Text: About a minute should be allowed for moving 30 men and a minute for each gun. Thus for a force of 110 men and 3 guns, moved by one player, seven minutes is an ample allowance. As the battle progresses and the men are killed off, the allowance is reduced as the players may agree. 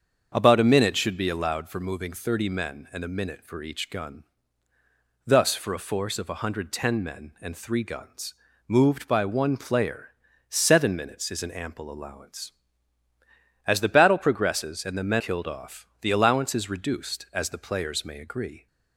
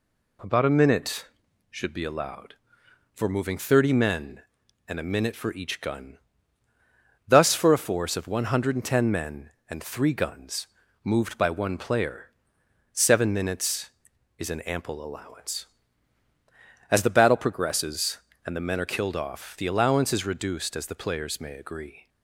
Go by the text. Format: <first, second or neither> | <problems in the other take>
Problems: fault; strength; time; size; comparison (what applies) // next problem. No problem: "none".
second | starts louder than the rest; until 1.3 s; 7 dB // skips "are"; at 15.1 s